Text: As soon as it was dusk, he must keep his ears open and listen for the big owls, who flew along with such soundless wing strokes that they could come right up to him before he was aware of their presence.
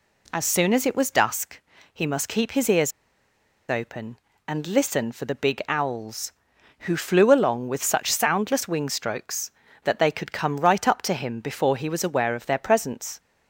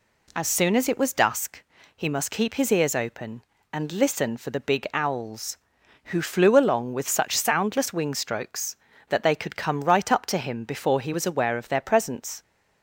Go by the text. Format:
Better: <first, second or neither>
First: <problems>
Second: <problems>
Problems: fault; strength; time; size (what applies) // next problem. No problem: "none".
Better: second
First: pauses between "ears" and "open"; noticeable; at 2.9 s; 0.78 s long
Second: none